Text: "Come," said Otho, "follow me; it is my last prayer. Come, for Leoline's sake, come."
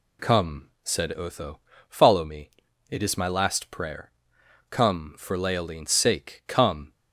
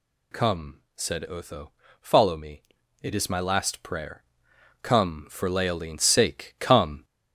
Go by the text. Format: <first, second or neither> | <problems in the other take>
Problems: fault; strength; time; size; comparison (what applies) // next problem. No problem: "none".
first | gets louder; noticeable; throughout; 4.5 dB